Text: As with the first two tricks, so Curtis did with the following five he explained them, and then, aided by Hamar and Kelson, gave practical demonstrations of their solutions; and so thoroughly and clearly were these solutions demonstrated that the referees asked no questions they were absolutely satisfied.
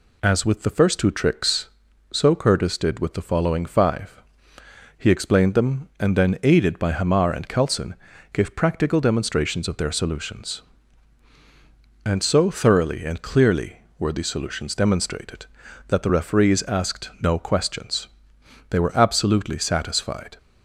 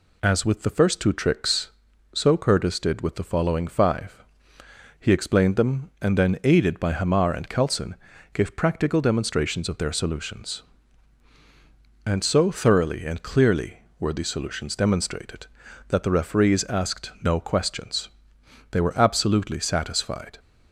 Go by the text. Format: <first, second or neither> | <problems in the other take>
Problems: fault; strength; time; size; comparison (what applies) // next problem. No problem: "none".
neither | pauses between "five" and "he"; noticeable; the same in both // pauses between "questions" and "they"; noticeable; the same in both